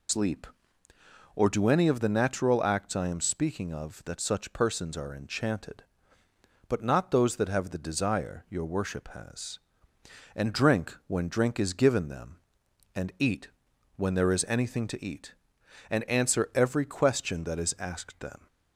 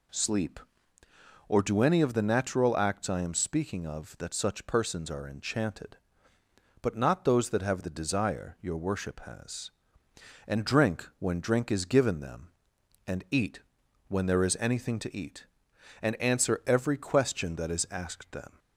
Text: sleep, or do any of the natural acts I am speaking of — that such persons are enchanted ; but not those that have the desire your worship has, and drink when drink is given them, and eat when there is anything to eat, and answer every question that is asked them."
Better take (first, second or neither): second